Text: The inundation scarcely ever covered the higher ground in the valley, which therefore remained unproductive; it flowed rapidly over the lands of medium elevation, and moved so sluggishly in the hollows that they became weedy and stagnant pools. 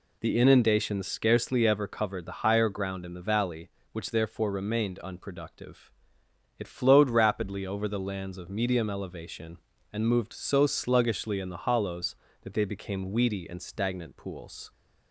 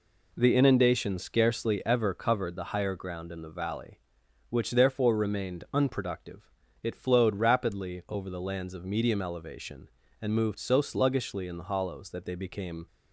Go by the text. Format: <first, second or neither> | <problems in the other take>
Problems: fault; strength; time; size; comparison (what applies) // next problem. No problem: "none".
first | stops before "weedy and stagnant pools"; at 12.8 s